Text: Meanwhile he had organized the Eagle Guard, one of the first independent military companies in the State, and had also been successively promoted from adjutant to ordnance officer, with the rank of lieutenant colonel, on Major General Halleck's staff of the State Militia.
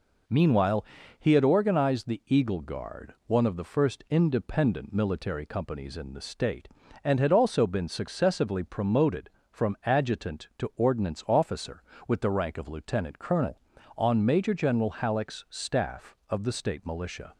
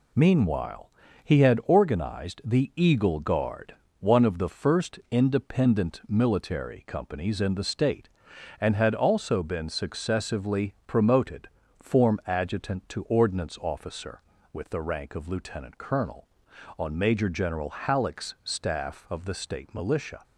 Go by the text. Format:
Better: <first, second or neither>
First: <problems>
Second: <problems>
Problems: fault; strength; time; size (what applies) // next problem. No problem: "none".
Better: first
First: pauses between "Meanwhile" and "he"; slight; at 0.8 s; 0.36 s long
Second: pauses between "Meanwhile" and "he"; slight; at 0.8 s; 0.34 s long // says "form" for "from"; at 11.7 s